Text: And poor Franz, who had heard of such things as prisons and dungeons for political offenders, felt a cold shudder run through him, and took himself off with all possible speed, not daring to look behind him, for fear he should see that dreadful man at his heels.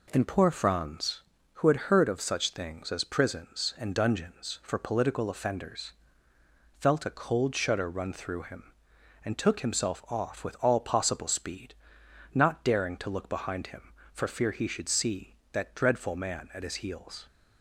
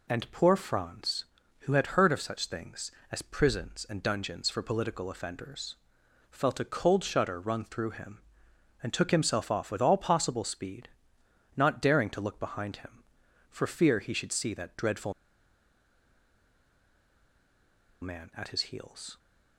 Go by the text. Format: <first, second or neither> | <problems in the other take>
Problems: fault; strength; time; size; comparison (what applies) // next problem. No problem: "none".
first | pauses between "dreadful" and "man"; strong; at 15.1 s; 2.8 s long